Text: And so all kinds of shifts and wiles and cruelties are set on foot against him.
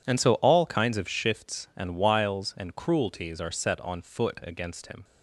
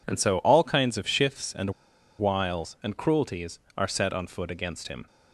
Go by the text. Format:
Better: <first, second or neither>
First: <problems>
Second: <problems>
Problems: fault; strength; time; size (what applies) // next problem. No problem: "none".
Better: first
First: none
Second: pauses between "and" and "wiles"; noticeable; at 1.7 s; 0.48 s long